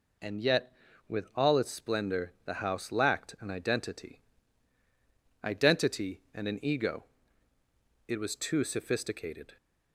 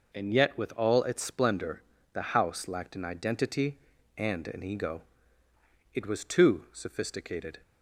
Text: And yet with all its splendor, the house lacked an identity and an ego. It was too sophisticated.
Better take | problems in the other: second | says "identity" twice; at 5.4 s

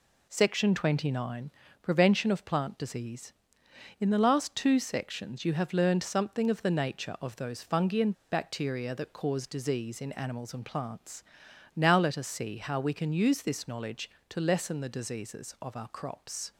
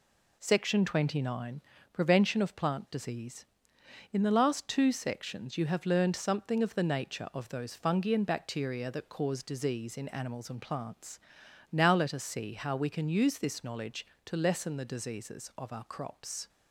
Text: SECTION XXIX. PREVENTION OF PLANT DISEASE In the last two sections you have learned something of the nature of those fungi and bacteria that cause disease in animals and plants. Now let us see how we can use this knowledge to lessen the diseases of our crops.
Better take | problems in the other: second | pauses between "and" and "bacteria"; slight; at 8.1 s; 0.19 s long

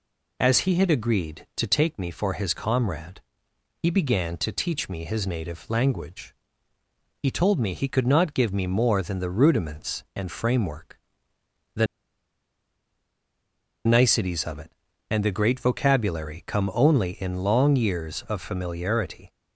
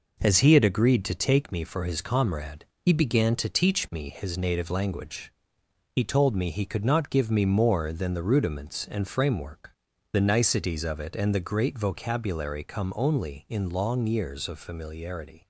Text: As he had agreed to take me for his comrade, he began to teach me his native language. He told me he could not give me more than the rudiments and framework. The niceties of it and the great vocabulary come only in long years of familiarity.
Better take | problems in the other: second | pauses between "The" and "niceties"; strong; at 11.8 s; 1.9 s long

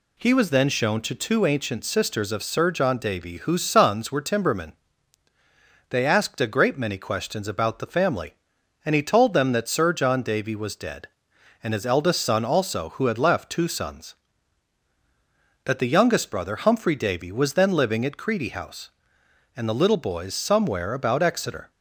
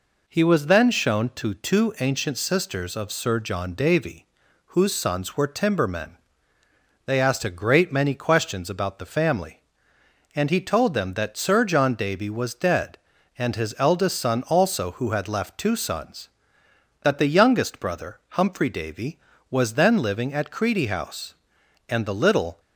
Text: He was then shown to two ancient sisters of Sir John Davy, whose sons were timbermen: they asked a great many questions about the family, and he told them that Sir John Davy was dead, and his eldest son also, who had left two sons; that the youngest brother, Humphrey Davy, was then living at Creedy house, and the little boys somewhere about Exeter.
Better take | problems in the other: first | stops before "boys somewhere about Exeter"; at 22.5 s

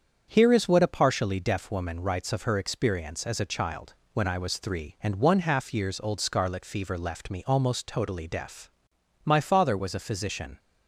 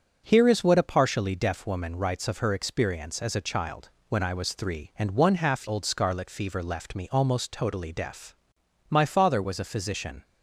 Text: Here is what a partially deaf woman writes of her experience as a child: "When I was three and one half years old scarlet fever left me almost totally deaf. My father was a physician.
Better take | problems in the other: first | starts louder than the rest; until 1.2 s; 6.5 dB; strong in the first // skips "years"; at 5.6 s

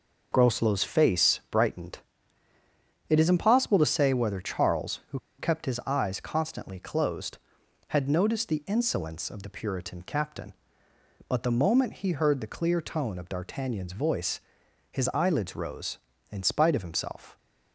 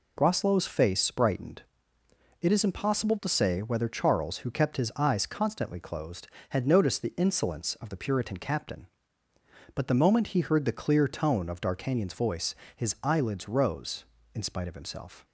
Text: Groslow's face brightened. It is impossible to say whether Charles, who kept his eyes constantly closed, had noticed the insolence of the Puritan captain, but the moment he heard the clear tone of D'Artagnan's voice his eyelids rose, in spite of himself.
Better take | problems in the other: second | pauses between "who" and "kept"; slight; at 5.1 s; 0.19 s long // pauses between "voice" and "his"; noticeable; at 14.4 s; 0.50 s long; slight in the second

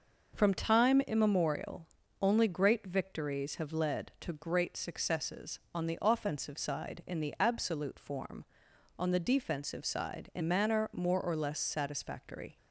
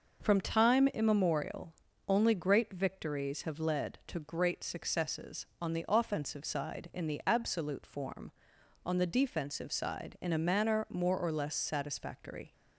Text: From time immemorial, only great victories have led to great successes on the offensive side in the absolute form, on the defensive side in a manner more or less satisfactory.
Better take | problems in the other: second | skips "a"; at 10.4 s

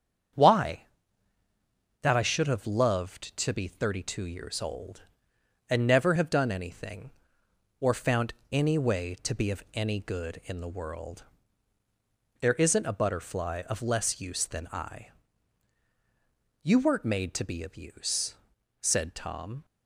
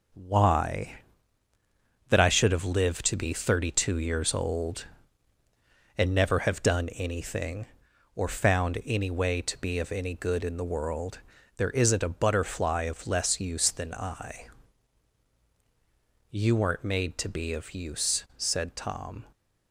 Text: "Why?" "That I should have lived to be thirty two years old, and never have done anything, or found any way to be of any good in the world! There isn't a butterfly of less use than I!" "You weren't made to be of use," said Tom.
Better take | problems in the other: second | starts louder than the rest; strong; until 2.5 s; 7.5 dB // says "loved" for "lived"; at 2.6 s // pauses between "found" and "any"; slight; at 8.3 s; 0.20 s long

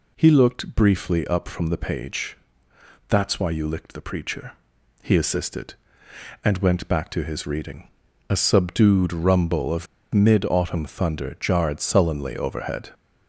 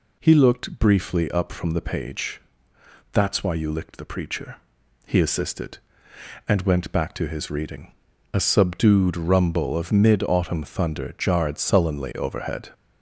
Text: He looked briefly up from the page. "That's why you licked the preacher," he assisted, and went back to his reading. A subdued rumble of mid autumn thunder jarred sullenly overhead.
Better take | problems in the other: second | pauses between "of" and "mid"; slight; at 9.8 s; 0.28 s long

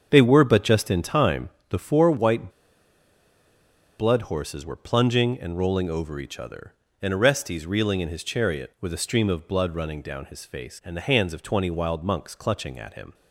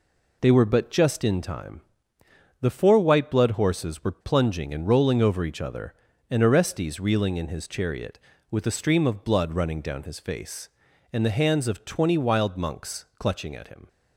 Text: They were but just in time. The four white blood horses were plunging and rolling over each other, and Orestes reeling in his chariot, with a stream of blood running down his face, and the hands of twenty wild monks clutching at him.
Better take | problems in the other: second | starts louder than the rest; until 1.1 s; 7 dB // pauses between "white" and "blood"; strong; at 2.4 s; 1.4 s long

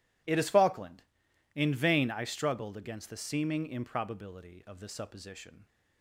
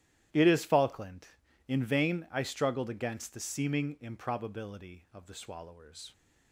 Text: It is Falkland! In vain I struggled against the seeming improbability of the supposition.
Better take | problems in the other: first | starts louder than the rest; strong; until 1.7 s; 13.5 dB // says "swallowers" for "supposition"; at 5.3 s

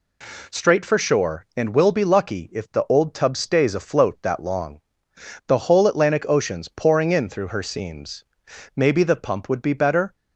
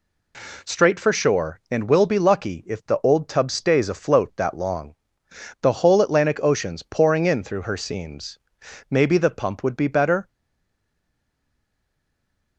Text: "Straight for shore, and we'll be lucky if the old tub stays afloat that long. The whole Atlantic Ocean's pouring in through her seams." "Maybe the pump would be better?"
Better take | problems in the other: first | stays silent after the last word; from 10.2 s on; 2.3 s long

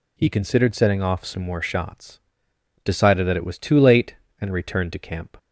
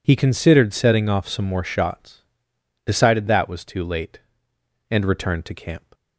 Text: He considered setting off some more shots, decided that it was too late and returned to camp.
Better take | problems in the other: first | skips "it"; at 3.4 s

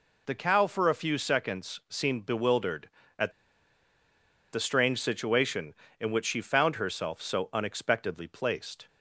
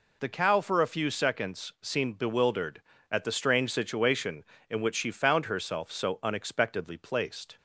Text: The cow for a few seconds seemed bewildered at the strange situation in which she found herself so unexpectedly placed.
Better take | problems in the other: second | pauses between "at" and "the"; at 3.3 s; 1.2 s long

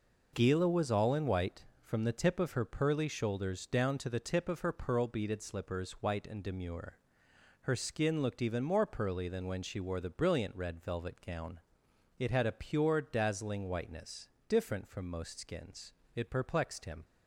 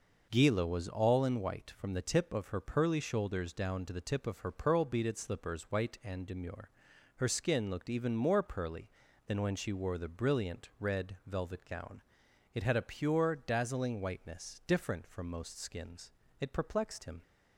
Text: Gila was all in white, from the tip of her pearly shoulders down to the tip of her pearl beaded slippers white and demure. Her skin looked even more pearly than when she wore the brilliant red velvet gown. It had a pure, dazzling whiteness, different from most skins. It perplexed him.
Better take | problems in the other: neither | none

